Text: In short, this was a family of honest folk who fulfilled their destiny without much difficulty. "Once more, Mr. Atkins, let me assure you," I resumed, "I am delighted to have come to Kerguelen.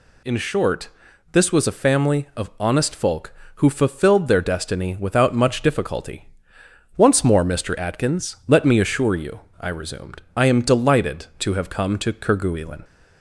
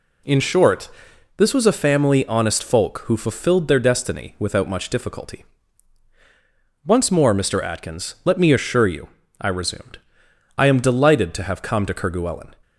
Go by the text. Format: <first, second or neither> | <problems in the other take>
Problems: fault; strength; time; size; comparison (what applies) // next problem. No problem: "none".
first | skips "of"; at 2.2 s